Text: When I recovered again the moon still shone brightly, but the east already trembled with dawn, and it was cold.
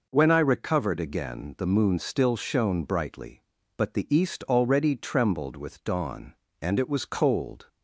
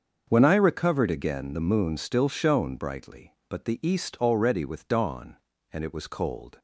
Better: first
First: none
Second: starts louder than the rest; until 1.2 s; 6.5 dB // skips "trembled"; at 4.6 s

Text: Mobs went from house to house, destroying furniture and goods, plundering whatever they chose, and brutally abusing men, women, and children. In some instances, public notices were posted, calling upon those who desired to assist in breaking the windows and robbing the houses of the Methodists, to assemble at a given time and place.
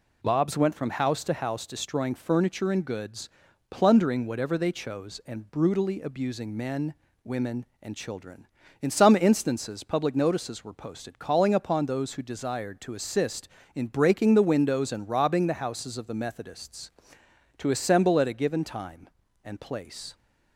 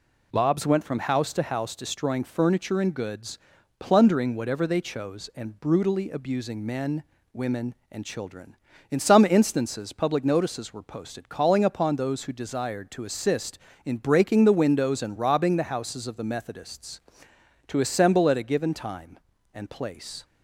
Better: neither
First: none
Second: none

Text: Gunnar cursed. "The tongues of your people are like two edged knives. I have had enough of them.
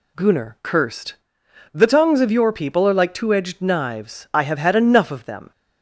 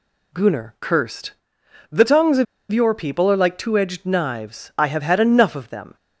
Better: first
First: none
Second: pauses between "of" and "your"; slight; at 2.4 s; 0.26 s long

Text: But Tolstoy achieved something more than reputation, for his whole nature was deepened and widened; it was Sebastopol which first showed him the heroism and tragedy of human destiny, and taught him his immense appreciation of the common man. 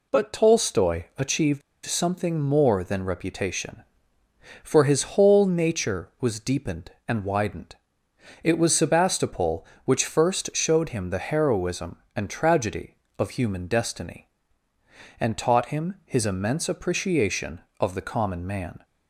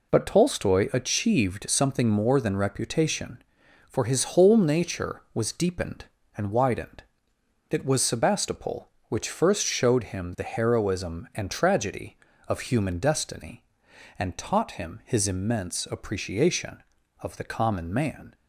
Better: second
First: pauses between "achieved" and "something"; slight; at 1.6 s; 0.24 s long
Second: none

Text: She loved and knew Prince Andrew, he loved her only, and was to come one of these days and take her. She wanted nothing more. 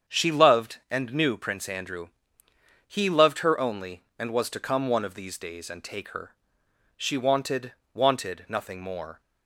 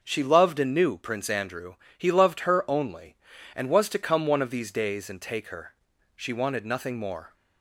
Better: second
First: starts louder than the rest; strong; until 1.2 s; 7.5 dB // says "wanted" twice; at 7.9 s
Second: none

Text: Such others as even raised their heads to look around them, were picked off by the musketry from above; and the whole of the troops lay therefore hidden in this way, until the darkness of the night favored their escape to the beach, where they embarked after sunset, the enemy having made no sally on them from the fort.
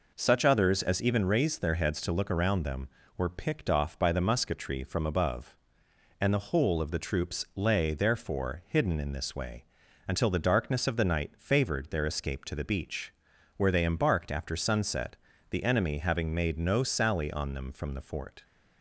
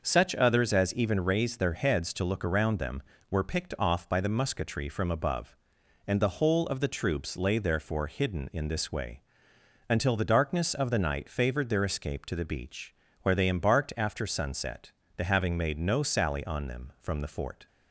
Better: first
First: none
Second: skips "enemy"; at 15.2 s

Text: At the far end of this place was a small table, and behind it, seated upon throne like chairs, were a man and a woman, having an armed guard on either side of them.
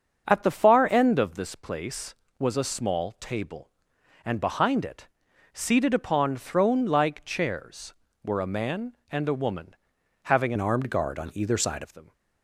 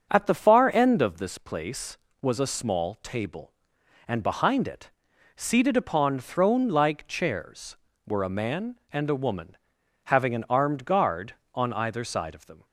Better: second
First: starts louder than the rest; until 1.3 s; 7 dB // changes voice from "an" to "side"; from 10.5 to 11.8 s; 1.3 s long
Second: starts louder than the rest; until 1.1 s; 7 dB

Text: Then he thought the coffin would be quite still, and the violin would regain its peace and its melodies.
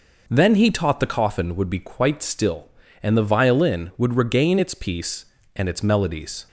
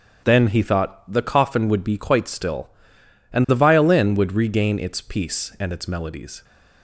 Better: second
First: says "taught" for "thought"; at 0.7 s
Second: none

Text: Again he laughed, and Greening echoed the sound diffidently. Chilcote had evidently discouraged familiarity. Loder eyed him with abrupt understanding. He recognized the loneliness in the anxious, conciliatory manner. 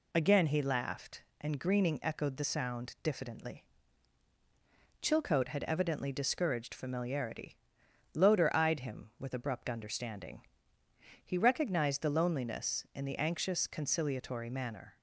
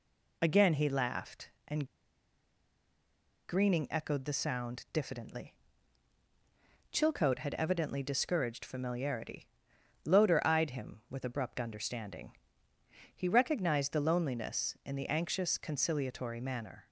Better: first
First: none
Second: pauses between "and" and "Greening"; strong; at 1.8 s; 1.6 s long

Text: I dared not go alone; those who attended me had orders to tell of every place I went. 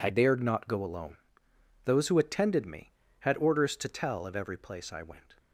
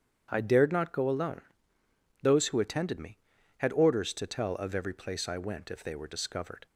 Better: first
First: none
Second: starts louder than the rest; strong; until 1.3 s; 8.5 dB // goes on to say "If they were discovered"; noticeable; from 5.7 s on; 0.94 s long

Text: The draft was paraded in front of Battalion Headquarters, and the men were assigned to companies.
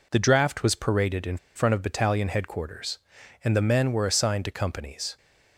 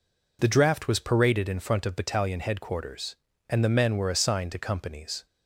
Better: second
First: pauses between "in" and "front"; slight; at 1.3 s; 0.19 s long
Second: none

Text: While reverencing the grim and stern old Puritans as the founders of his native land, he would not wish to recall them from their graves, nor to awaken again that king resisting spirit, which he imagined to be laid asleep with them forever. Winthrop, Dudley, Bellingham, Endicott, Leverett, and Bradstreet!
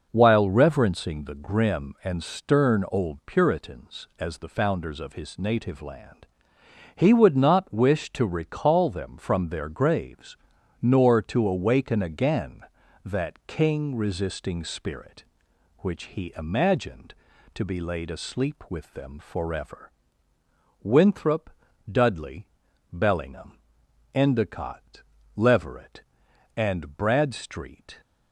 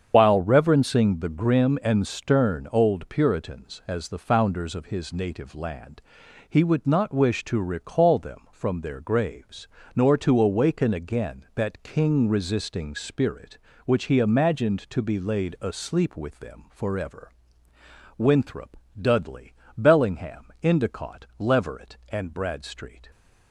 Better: first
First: none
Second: loses the start of "While"; at 0.1 s; 65 ms // starts louder than the rest; strong; until 1.1 s; 7.5 dB

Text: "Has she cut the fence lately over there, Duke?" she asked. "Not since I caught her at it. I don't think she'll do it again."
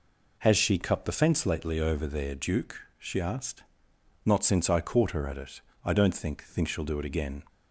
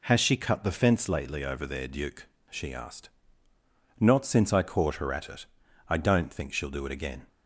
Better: second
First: says "think" twice; at 6.4 s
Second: none

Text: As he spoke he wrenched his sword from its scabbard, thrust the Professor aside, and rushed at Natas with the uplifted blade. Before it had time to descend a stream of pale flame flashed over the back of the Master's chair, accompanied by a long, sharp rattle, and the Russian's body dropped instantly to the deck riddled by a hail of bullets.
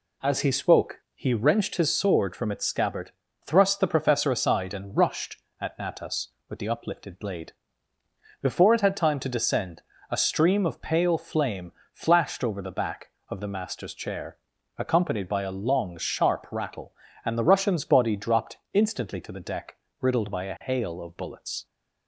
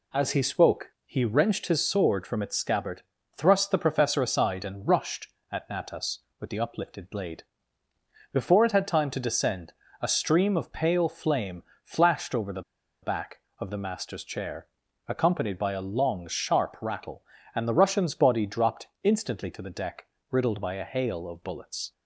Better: first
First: pauses between "descend" and "a"; slight; at 9.8 s; 0.30 s long // pauses between "flame" and "flashed"; slight; at 11.7 s; 0.22 s long // pauses between "dropped" and "instantly"; slight; at 18.5 s; 0.16 s long // pauses between "deck" and "riddled"; slight; at 19.7 s; 0.24 s long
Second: pauses between "descend" and "a"; slight; at 9.7 s; 0.30 s long // pauses between "flame" and "flashed"; slight; at 11.6 s; 0.22 s long // pauses between "the" and "back"; at 12.6 s; 0.41 s long // pauses between "dropped" and "instantly"; slight; at 18.8 s; 0.16 s long // pauses between "deck" and "riddled"; slight; at 20.0 s; 0.24 s long

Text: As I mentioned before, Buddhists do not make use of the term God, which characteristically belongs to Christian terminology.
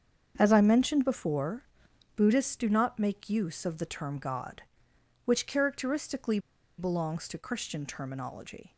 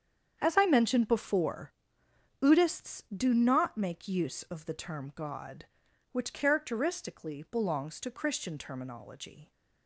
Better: second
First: starts louder than the rest; strong; until 1.3 s; 7.5 dB // pauses between "characteristically" and "belongs"; at 6.3 s; 0.40 s long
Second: starts louder than the rest; strong; until 1.4 s; 8 dB

